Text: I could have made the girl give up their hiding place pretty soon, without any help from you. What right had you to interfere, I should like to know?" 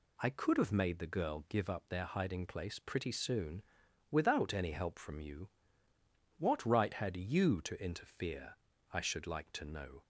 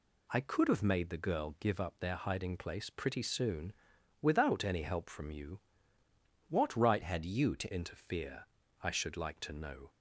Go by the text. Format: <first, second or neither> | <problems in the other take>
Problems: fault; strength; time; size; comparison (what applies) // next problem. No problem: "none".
first | changes voice from "had" to "to"; from 7.0 to 7.7 s; 0.7 s long